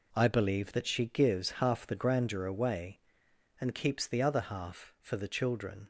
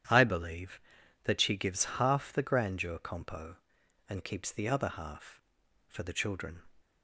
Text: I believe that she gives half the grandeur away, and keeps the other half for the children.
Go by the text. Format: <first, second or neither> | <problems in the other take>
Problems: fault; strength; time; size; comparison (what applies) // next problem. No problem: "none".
first | starts louder than the rest; strong; until 1.5 s; 10 dB // says "compo" for "away"; at 2.9 s